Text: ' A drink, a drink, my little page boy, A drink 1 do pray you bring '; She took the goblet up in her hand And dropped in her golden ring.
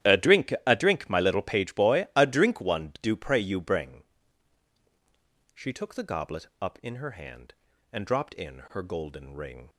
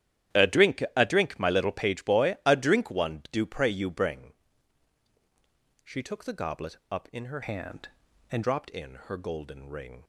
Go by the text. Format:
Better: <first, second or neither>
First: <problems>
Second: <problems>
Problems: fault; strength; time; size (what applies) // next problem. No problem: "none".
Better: first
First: starts louder than the rest; strong; until 1.1 s; 12.5 dB // pauses between "in" and "her"; slight; at 8.5 s; 0.17 s long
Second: starts louder than the rest; strong; until 1.4 s; 12.5 dB // changes voice from "hand" to "And"; from 7.4 to 8.4 s; 1.0 s long // pauses between "in" and "her"; slight; at 8.9 s; 0.16 s long